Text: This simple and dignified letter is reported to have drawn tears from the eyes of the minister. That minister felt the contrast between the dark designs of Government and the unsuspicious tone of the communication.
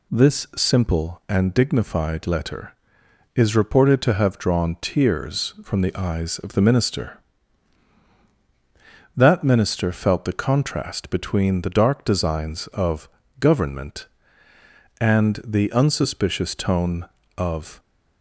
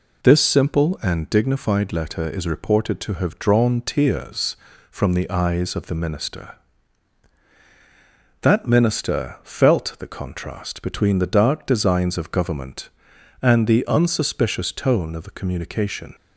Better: second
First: pauses between "of" and "Government"; slight; at 13.0 s; 0.32 s long // stops before "the communication"; at 17.7 s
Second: none

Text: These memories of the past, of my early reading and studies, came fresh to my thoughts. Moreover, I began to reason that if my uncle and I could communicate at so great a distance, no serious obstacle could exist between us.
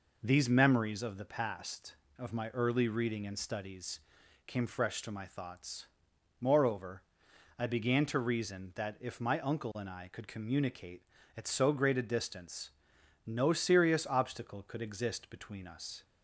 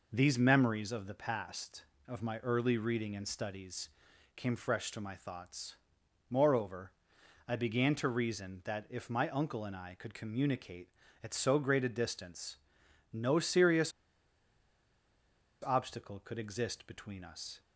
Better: first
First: none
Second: pauses between "serious" and "obstacle"; strong; at 13.9 s; 1.7 s long

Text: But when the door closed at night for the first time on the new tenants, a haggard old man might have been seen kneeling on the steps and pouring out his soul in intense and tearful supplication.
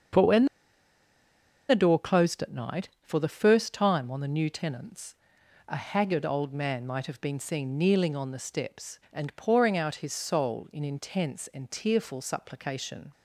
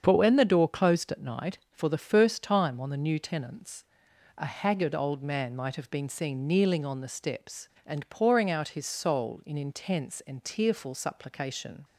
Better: second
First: starts louder than the rest; strong; until 2.3 s; 7.5 dB // pauses between "when" and "the"; at 0.4 s; 1.2 s long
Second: starts louder than the rest; strong; until 1.0 s; 7.5 dB

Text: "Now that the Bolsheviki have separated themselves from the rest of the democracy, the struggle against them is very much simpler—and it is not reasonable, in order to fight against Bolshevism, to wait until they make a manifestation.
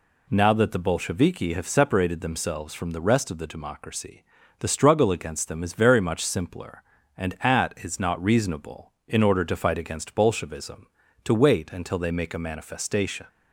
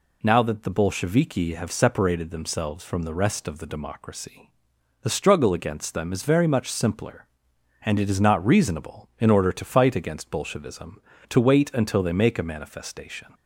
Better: second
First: says "at" for "it"; at 7.4 s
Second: none

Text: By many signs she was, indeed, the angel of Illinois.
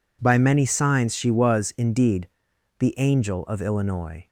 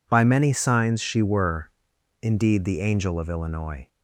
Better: first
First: none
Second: says "were" for "was"; at 1.2 s

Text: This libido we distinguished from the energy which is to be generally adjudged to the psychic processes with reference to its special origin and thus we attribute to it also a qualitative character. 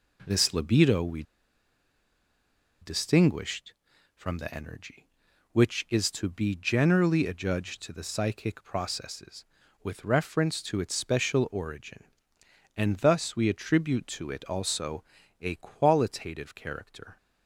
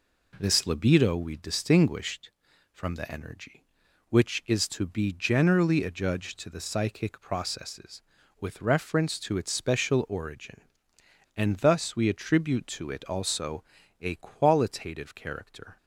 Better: second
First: pauses between "we" and "distinguished"; strong; at 1.2 s; 1.5 s long // pauses between "also" and "a"; at 15.0 s; 0.38 s long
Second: pauses between "also" and "a"; at 13.6 s; 0.38 s long

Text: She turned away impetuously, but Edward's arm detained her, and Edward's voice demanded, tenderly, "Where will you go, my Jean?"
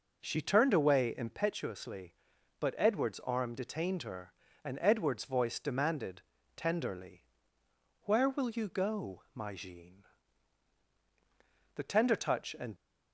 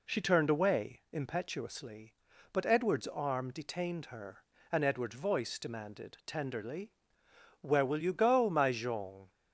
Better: second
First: goes on to say "The tender touch and"; noticeable; from 11.7 s on; 0.99 s long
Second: none

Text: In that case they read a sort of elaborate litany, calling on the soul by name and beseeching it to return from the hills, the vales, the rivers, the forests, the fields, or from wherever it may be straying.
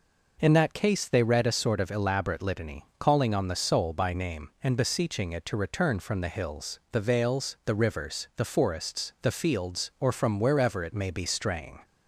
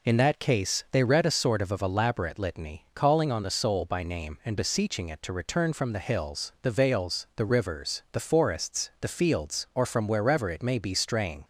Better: first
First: none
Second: says "of" twice; at 1.7 s

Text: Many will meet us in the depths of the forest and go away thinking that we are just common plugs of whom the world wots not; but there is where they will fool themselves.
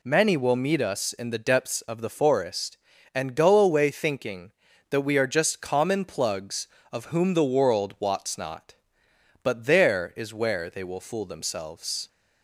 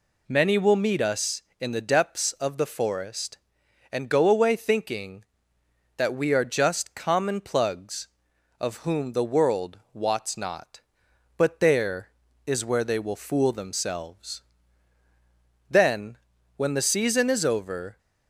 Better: first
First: none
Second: pauses between "world" and "wots"; slight; at 9.7 s; 0.16 s long // goes on to say "Then when the season is over"; strong; from 15.6 s on; 2.2 s long

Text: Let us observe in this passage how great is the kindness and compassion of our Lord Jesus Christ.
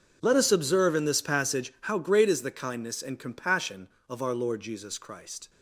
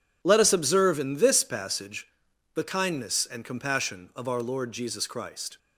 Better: first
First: none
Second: skips "how great is"; at 2.3 s

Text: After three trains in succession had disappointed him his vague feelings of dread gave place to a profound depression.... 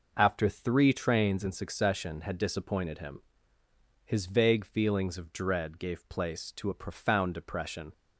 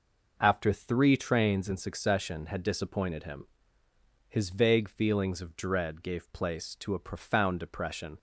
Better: neither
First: pauses between "him" and "his"; noticeable; at 3.2 s; 0.82 s long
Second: pauses between "him" and "his"; noticeable; at 3.4 s; 0.80 s long

